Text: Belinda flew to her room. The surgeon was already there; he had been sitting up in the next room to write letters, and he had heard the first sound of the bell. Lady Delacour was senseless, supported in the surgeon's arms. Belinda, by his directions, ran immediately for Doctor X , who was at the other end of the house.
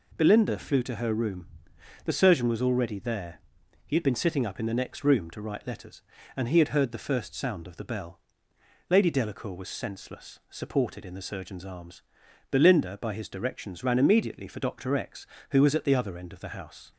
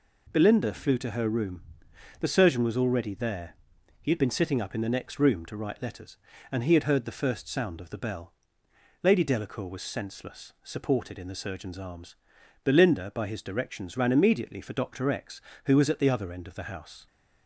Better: neither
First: none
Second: none

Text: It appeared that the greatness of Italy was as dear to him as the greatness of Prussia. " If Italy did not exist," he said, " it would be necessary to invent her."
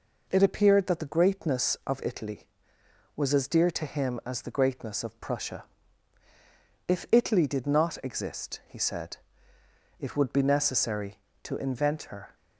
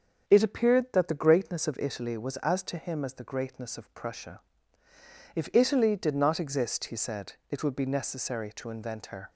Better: first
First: none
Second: starts louder than the rest; until 1.2 s; 7 dB // skips "dear"; at 2.6 s

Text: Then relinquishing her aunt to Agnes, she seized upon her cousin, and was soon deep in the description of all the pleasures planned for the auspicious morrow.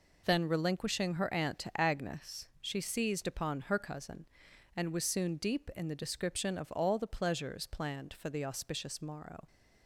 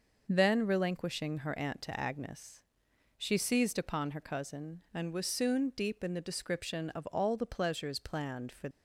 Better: first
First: none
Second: stops before "the auspicious morrow"; at 8.7 s

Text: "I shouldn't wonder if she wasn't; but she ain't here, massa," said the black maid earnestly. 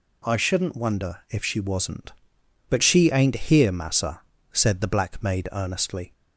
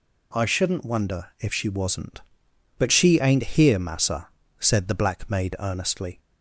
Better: neither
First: none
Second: none

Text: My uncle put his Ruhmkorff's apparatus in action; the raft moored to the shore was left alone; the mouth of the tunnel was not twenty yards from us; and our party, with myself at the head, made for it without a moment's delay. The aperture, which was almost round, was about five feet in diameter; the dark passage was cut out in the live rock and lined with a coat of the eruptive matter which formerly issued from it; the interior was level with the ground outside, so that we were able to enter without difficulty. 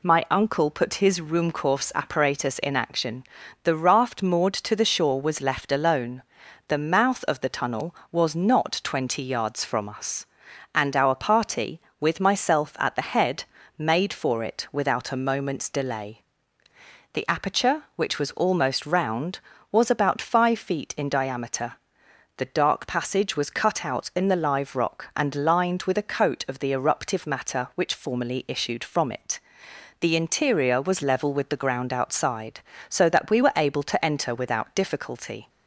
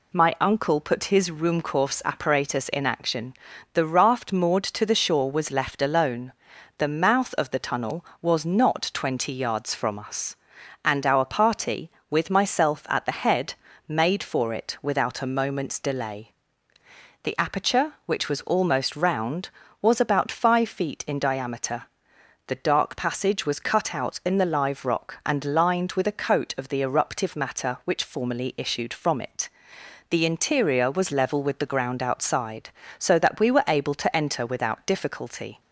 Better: neither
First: none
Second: none

